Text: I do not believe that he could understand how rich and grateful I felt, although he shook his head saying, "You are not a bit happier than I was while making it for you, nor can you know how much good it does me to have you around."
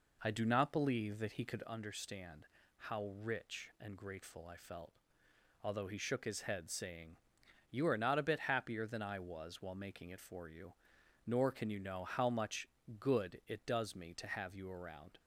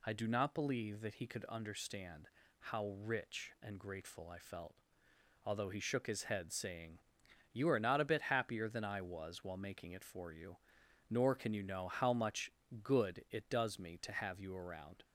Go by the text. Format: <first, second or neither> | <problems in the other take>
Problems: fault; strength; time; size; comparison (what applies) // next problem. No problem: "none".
second | starts louder than the rest; noticeable; until 1.7 s; 4 dB // pauses between "understand" and "how"; slight; at 2.4 s; 0.30 s long; slight in the second // pauses between "much" and "good"; slight; at 12.6 s; 0.32 s long; slight in the second